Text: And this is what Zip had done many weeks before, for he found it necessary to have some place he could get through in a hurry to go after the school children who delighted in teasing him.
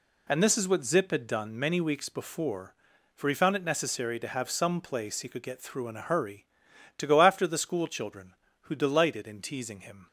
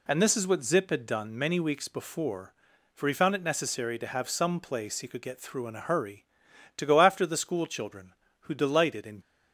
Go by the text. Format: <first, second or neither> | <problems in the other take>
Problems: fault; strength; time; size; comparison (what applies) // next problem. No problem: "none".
first | stops before "teasing him"; at 9.2 s